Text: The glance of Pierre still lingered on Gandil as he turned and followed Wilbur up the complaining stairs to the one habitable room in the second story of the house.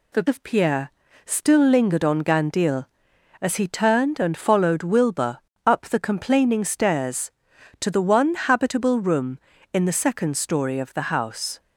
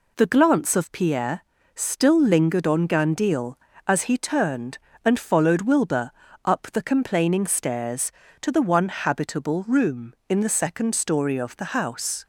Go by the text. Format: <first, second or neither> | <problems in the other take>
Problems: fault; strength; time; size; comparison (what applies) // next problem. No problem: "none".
second | skips "glance"; at 0.2 s // pauses between "Pierre" and "still"; slight; at 0.9 s; 0.34 s long; slight in the second // pauses between "Wilbur" and "up"; slight; at 5.3 s; 0.26 s long; slight in the second